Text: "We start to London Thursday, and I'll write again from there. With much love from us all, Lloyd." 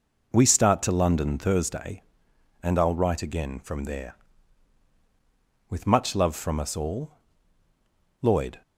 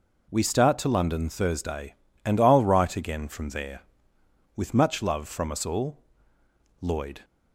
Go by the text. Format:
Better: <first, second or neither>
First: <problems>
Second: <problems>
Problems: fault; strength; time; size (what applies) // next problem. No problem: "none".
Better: neither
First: none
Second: none